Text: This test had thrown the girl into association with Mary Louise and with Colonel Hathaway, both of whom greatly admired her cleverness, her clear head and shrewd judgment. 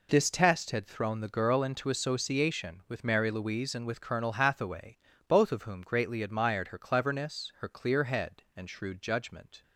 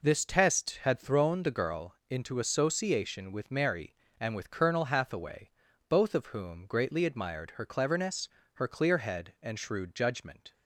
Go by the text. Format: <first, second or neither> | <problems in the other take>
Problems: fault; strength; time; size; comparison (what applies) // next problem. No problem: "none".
first | skips "Louise"; at 4.0 s